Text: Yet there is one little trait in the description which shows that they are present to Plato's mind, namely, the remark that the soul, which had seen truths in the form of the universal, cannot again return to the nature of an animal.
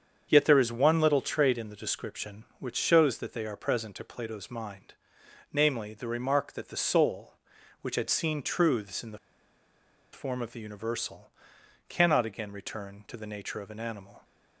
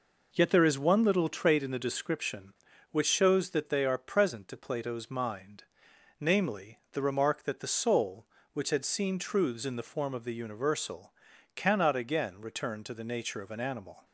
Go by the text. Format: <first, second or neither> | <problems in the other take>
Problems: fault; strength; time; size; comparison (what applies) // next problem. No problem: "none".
second | starts louder than the rest; strong; until 1.3 s; 7.5 dB // pauses between "the" and "form"; noticeable; at 9.1 s; 0.95 s long